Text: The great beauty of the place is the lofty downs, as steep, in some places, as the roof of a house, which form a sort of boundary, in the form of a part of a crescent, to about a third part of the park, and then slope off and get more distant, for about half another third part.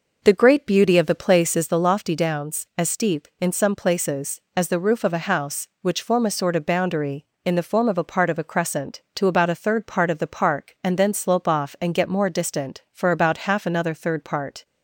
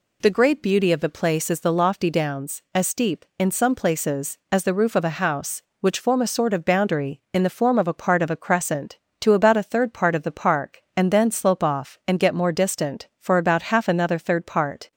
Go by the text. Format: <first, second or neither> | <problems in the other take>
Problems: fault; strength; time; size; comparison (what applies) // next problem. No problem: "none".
second | starts louder than the rest; noticeable; until 1.7 s; 5.5 dB